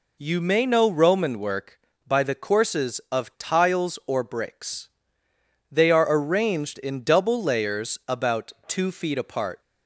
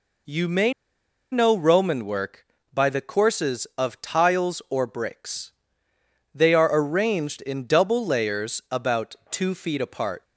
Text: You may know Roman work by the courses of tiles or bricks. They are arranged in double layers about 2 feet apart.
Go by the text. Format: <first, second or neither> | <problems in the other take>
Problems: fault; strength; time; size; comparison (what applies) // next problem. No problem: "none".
first | pauses between "may" and "know"; noticeable; at 0.7 s; 0.59 s long